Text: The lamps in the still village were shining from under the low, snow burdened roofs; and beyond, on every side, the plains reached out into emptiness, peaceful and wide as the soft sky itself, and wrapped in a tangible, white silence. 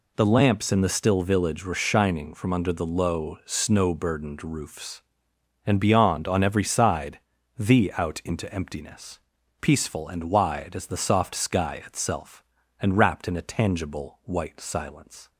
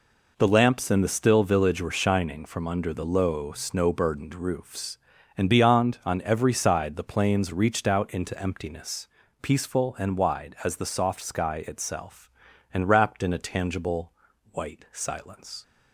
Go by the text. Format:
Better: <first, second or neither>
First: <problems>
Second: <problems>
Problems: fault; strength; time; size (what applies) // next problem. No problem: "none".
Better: second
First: skips "plains reached"; at 7.9 s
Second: none